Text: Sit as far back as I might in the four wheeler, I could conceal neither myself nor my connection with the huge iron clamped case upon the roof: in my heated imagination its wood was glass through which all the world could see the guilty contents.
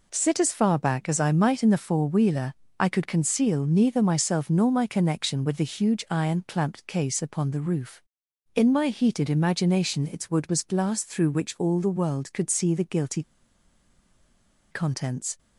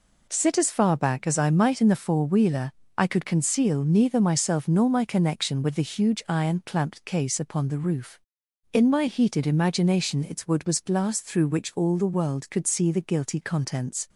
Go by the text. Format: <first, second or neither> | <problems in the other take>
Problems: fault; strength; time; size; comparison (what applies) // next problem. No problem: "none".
second | pauses between "guilty" and "contents"; strong; at 13.2 s; 1.4 s long